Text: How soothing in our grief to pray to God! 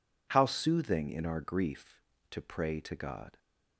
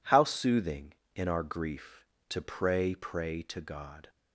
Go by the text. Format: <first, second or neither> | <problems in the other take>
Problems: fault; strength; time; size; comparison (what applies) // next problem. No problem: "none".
first | says "pray" twice; at 2.9 s